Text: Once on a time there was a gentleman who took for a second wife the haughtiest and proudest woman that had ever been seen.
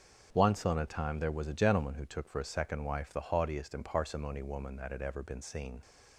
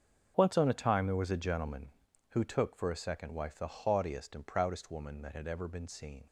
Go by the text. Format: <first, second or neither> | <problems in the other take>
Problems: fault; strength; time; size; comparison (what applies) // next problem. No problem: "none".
second | starts louder than the rest; until 1.3 s; 6.5 dB; also in the second // says "parsimony" for "proudest"; at 3.8 s